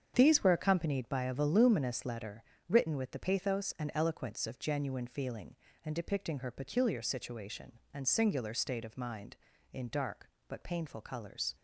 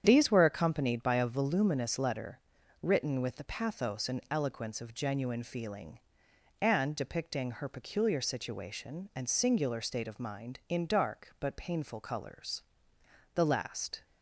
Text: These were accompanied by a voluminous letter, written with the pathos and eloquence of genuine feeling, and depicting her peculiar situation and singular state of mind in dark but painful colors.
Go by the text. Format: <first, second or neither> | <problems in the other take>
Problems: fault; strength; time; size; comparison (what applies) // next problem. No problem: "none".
first | starts louder than the rest; strong; until 1.0 s; 8.5 dB; strong in the first // goes on to say "The last"; noticeable; from 13.3 s on; 0.70 s long